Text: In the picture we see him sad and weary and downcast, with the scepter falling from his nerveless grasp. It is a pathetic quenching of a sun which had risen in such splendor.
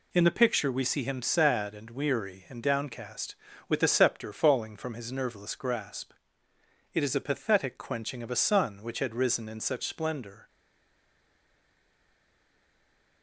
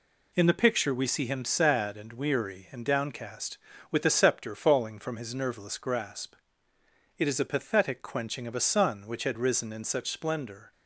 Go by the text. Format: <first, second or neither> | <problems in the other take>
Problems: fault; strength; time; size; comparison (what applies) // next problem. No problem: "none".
second | stays silent after the last word; strong; from 10.4 s on; 2.8 s long